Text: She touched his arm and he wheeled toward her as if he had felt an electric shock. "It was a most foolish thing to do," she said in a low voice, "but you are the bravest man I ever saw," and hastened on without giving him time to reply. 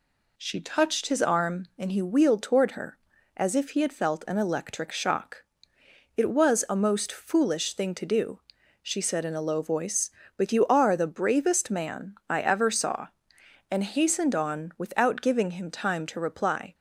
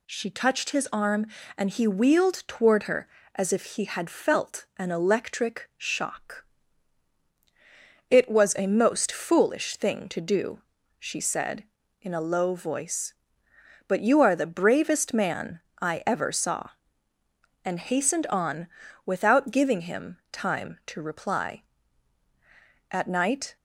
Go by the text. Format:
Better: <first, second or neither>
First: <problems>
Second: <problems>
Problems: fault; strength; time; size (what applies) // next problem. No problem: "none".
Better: first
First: none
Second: pauses between "man" and "I"; slight; at 15.5 s; 0.22 s long // pauses between "on" and "without"; at 18.6 s; 0.38 s long // goes on to say "At night"; noticeable; from 22.9 s on; 0.64 s long